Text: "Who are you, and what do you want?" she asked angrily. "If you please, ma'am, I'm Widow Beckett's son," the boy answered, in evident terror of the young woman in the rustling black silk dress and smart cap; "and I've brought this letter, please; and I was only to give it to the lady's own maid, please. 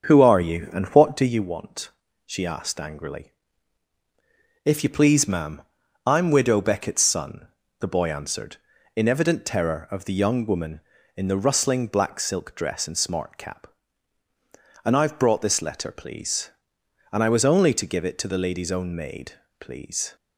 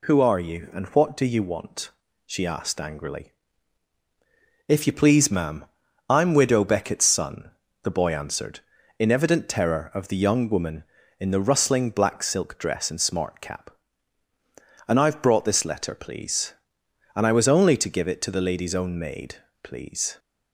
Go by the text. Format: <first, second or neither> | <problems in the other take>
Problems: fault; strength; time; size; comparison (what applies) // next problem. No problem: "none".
second | starts louder than the rest; until 1.3 s; 7 dB